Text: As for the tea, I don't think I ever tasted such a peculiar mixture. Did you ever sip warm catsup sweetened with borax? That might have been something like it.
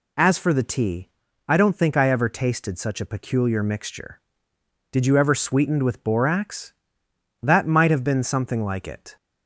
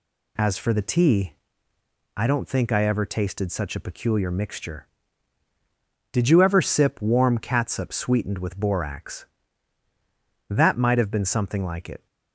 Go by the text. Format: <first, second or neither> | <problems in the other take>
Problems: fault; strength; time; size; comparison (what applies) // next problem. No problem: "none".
second | skips "sip warm catsup"; at 5.3 s